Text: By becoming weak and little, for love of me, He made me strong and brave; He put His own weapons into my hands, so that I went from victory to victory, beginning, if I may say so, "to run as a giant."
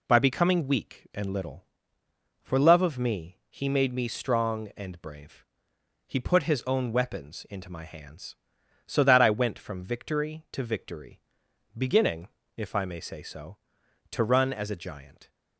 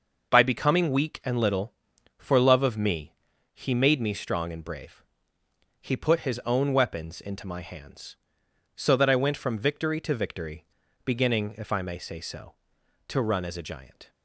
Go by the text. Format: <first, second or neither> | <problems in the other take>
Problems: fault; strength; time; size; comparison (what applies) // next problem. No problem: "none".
neither | none